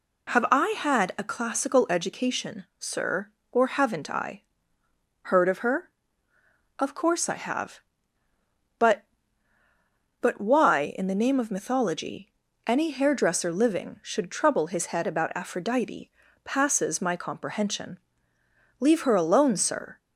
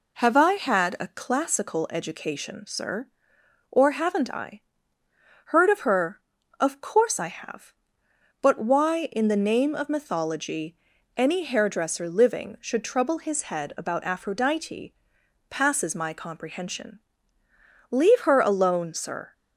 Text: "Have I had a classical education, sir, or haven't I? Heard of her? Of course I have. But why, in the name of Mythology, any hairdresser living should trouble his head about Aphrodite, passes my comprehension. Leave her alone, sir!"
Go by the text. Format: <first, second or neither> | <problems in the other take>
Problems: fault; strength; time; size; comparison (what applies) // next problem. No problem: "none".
second | says "But" twice; at 10.2 s